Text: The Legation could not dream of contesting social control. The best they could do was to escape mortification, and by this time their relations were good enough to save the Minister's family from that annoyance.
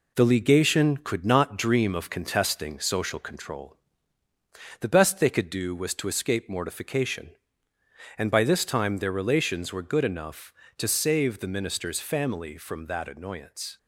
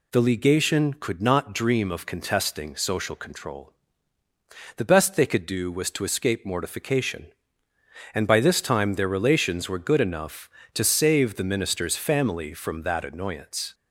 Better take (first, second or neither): second